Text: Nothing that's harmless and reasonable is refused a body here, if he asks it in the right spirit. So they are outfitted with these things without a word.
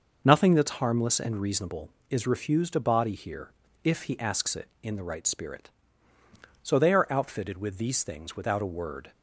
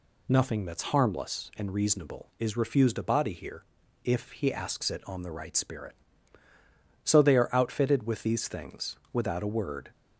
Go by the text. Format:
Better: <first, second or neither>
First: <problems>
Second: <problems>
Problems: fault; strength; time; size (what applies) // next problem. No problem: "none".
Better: first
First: none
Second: says "on" for "in"; at 5.0 s // pauses between "things" and "without"; slight; at 8.9 s; 0.16 s long